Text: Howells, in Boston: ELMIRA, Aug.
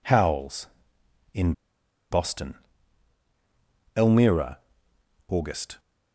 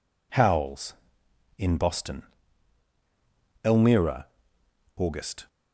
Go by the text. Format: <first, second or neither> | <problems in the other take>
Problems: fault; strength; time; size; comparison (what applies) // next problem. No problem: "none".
second | pauses between "in" and "Boston"; noticeable; at 1.5 s; 0.57 s long